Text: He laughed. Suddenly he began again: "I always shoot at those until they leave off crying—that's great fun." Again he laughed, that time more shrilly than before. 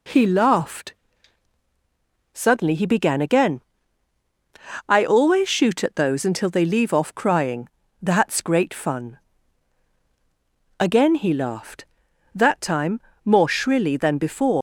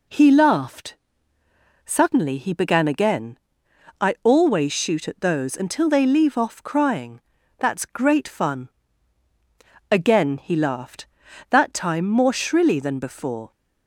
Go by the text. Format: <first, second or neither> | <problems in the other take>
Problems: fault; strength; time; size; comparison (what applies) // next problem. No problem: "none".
second | pauses between "time" and "more"; slight; at 13.0 s; 0.24 s long // leaves "before" unfinished; at 14.5 s; 140 ms